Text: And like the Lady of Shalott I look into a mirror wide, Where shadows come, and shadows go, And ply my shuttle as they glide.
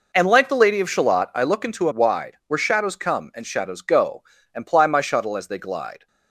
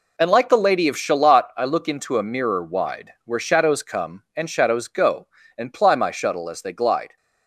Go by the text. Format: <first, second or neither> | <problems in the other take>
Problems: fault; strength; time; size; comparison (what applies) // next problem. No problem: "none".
second | skips "mirror"; at 1.9 s